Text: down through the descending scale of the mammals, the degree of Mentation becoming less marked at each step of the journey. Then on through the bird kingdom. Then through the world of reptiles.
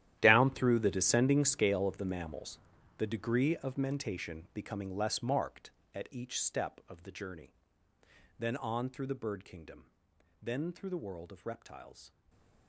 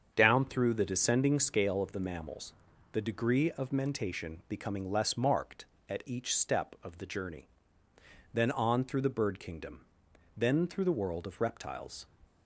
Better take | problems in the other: second | gets quieter; strong; throughout; 16 dB // starts louder than the rest; strong; until 1.2 s; 12 dB; strong in the second // stays silent after the last word; slight; from 12.0 s on; 0.6 s long

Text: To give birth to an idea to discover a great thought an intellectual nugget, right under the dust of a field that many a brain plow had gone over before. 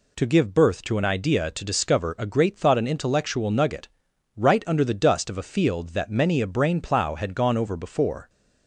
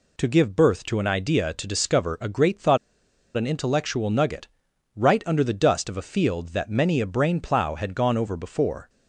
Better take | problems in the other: first | pauses between "thought" and "an"; noticeable; at 2.7 s; 0.59 s long

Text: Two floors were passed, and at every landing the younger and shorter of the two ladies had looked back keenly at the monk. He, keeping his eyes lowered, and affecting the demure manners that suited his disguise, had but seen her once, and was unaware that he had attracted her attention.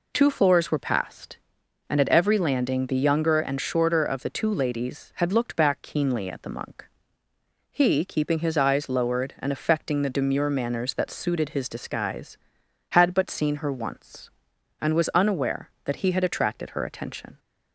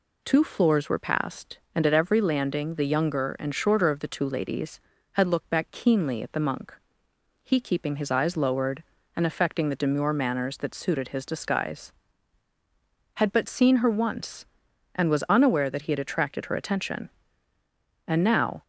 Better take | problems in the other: first | goes on to say "And now"; from 18.0 s on; 0.56 s long

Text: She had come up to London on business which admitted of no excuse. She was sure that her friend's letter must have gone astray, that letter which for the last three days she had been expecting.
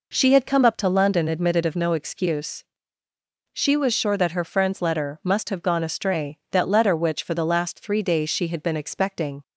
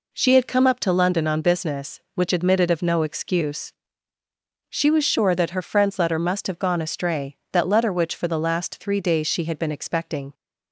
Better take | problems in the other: second | skips "on business which"; at 1.2 s

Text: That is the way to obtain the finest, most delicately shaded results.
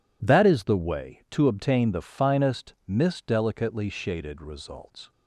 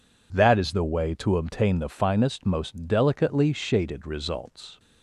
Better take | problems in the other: second | says "mist" for "most"; at 2.8 s

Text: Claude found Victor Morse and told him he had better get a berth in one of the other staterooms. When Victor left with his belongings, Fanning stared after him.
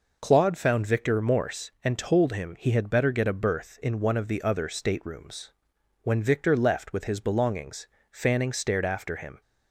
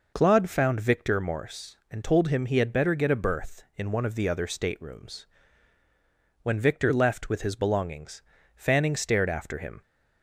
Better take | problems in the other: neither | none

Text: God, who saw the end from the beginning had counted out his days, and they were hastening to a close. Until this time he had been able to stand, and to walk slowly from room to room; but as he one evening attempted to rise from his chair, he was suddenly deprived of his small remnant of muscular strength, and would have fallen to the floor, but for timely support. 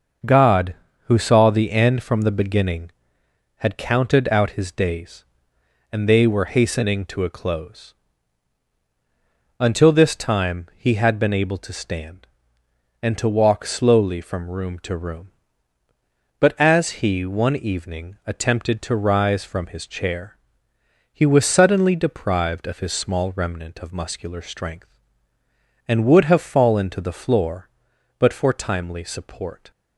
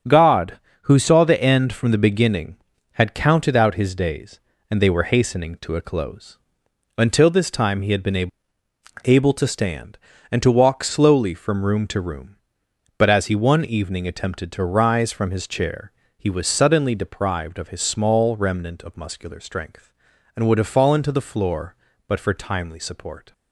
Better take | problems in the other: first | starts louder than the rest; until 1.3 s; 7 dB; noticeable in the first // says "able" twice; at 9.0 s

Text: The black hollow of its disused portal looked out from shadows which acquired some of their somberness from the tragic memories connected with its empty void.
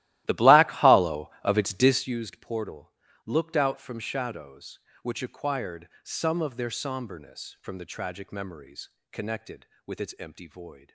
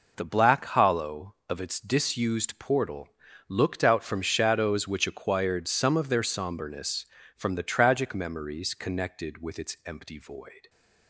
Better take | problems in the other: second | starts louder than the rest; strong; until 2.2 s; 15.5 dB // pauses between "portal" and "looked"; slight; at 2.9 s; 0.34 s long; also in the second // pauses between "acquired" and "some"; slight; at 5.8 s; 0.16 s long // pauses between "memories" and "connected"; slight; at 8.9 s; 0.20 s long

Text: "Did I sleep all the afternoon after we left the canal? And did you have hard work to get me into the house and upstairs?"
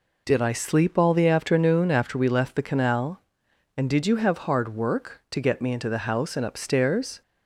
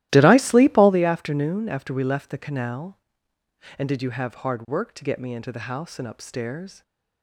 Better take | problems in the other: first | starts louder than the rest; strong; until 1.0 s; 15 dB

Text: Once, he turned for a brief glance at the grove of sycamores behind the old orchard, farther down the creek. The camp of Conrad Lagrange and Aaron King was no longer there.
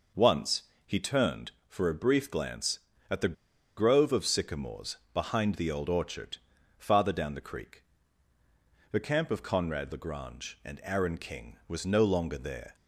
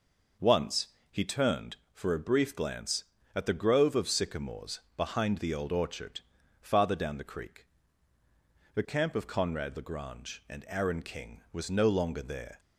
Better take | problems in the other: second | pauses between "the" and "grove"; at 3.3 s; 0.41 s long // pauses between "sycamores" and "behind"; slight; at 4.9 s; 0.18 s long; slight in the second

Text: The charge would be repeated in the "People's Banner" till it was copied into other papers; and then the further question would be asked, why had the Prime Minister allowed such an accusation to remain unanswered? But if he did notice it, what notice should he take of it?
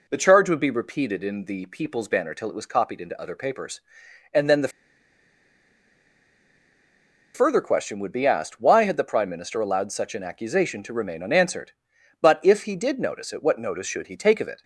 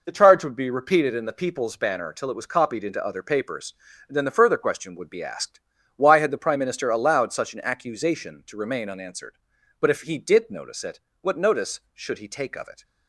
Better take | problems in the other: second | pauses between "the" and "further"; strong; at 4.6 s; 2.6 s long

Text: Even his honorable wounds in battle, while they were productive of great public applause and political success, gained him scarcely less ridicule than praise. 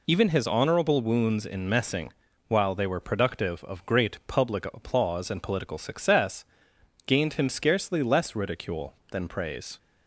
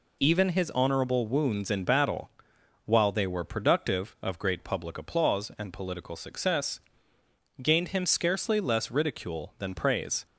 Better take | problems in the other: second | says "messing" for "battle"; at 1.6 s

